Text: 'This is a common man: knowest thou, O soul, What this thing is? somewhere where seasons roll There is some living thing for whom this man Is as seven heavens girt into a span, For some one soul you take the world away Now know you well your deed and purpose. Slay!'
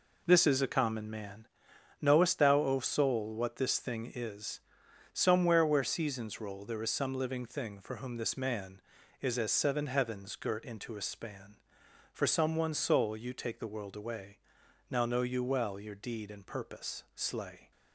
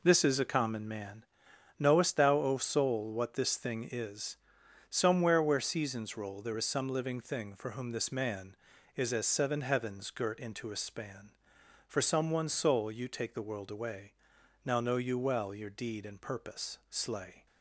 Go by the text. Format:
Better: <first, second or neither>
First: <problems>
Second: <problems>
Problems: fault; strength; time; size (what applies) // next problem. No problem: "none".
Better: neither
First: pauses between "away" and "Now"; noticeable; at 14.3 s; 0.52 s long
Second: pauses between "away" and "Now"; noticeable; at 14.1 s; 0.52 s long